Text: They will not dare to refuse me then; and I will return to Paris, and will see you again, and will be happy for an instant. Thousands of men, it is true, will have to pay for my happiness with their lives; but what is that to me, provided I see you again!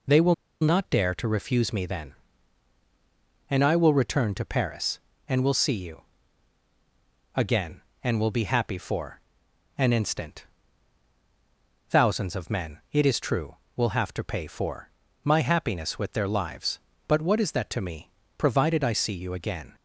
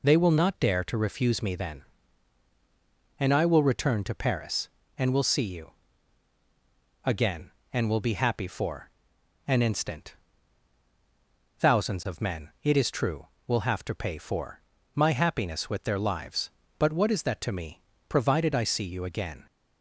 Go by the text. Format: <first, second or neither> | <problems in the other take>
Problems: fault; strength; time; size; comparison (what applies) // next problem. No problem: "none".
second | pauses between "will" and "not"; slight; at 0.3 s; 0.27 s long // pauses between "you" and "again"; strong; at 6.0 s; 1.3 s long; strong in the second // pauses between "for" and "an"; noticeable; at 9.1 s; 0.58 s long; noticeable in the second // pauses between "for" and "my"; slight; at 14.8 s; 0.36 s long; slight in the second